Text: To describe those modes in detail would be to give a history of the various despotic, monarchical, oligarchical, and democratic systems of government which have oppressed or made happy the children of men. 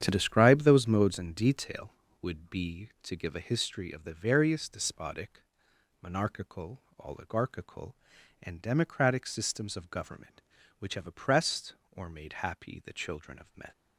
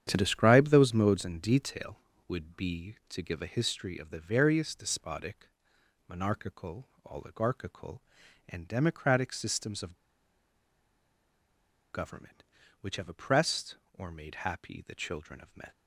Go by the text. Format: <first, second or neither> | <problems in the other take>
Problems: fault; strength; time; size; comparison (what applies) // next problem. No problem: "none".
first | starts louder than the rest; strong; until 1.0 s; 9 dB; strong in the first // pauses between "of" and "government"; strong; at 9.9 s; 1.9 s long